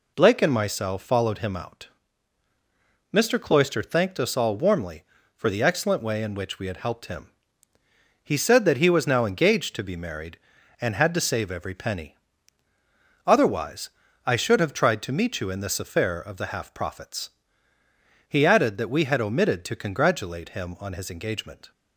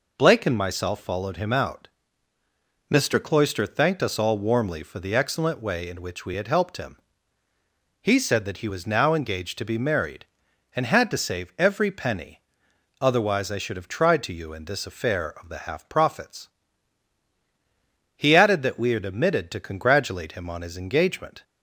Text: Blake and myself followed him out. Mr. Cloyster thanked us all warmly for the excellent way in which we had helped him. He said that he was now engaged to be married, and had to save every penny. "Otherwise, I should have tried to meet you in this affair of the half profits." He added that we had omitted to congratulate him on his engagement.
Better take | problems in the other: first | skips "meet"; at 14.3 s

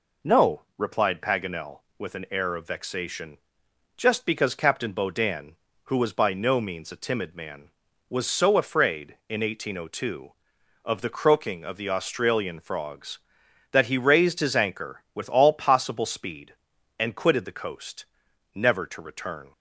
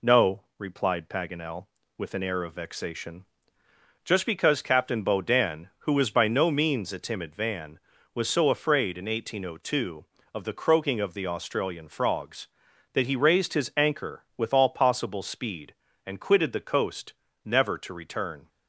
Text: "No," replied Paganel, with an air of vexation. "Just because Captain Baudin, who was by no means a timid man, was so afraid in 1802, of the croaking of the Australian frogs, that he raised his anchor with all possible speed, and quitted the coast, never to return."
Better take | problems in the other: first | says "van" for "man"; at 7.3 s

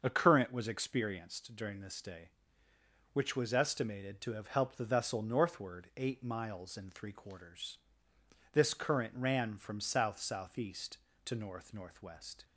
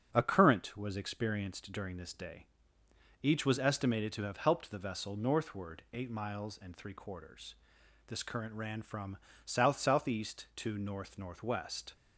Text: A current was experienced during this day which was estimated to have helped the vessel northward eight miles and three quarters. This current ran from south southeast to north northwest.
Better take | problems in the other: first | starts louder than the rest; strong; until 1.1 s; 7.5 dB; also in the first // says "each" for "which"; at 3.2 s // pauses between "from" and "south"; slight; at 9.1 s; 0.28 s long

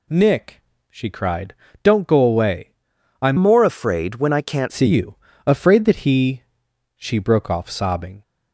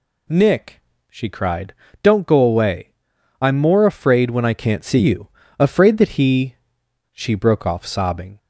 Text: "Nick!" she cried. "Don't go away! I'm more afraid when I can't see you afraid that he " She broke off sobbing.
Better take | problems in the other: second | changes voice from "more" to "can't"; from 3.3 to 4.7 s; 1.4 s long // pauses between "you" and "afraid"; slight; at 5.1 s; 0.30 s long; slight in the second

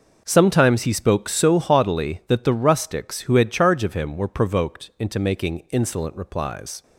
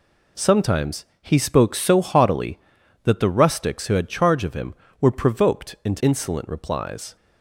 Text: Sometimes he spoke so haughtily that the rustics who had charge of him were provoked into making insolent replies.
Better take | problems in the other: first | pauses between "Sometimes" and "he"; slight; at 1.0 s; 0.16 s long // skips "making"; at 6.0 s

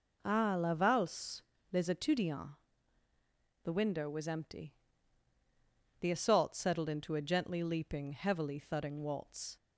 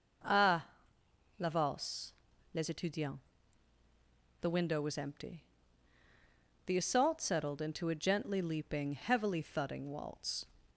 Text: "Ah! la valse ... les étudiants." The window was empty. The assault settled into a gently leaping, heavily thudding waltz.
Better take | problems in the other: neither | none

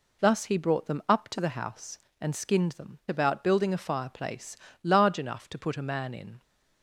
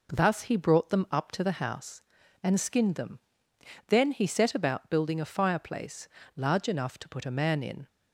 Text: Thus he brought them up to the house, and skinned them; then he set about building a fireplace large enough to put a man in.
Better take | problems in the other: second | skips "then he set"; at 3.0 s // pauses between "fireplace" and "large"; slight; at 4.5 s; 0.26 s long; slight in the second

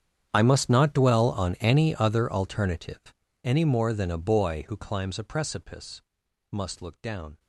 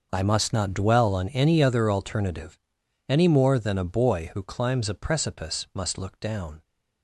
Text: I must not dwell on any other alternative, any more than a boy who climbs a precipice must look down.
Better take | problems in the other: second | gets quieter; strong; throughout; 22 dB // pauses between "precipice" and "must"; noticeable; at 6.0 s; 0.48 s long

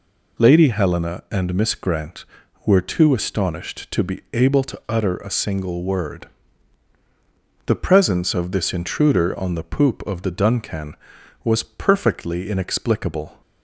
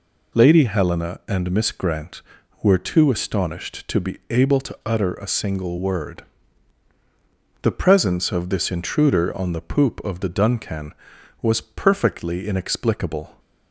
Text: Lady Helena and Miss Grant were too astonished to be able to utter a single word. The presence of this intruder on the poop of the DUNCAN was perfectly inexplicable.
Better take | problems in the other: neither | none

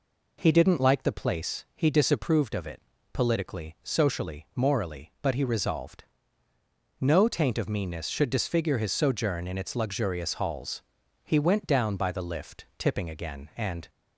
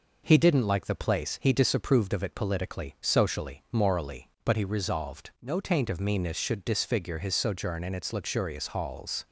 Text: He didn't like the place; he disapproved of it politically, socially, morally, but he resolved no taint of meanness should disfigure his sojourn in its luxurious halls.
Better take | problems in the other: second | pauses between "it" and "politically"; slight; at 2.8 s; 0.30 s long // pauses between "resolved" and "no"; noticeable; at 6.0 s; 0.96 s long // goes on to say "He went down by the lift tipping again and"; strong; from 11.2 s on; 2.6 s long

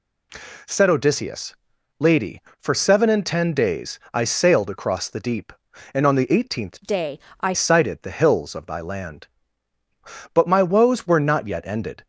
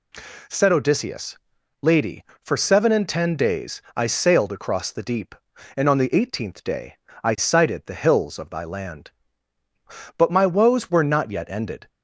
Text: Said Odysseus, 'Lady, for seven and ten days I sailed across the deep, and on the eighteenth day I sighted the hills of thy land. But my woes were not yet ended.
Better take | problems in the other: second | changes voice from "day" to "I"; from 6.8 to 7.5 s; 0.7 s long // pauses between "day" and "I"; slight; at 7.1 s; 0.22 s long; slight in the second

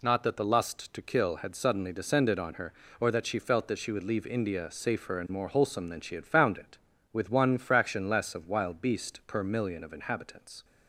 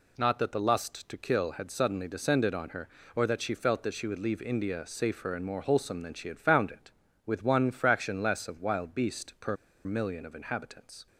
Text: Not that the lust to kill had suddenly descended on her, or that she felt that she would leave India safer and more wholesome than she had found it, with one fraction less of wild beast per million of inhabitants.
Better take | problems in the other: first | pauses between "per" and "million"; slight; at 9.5 s; 0.29 s long

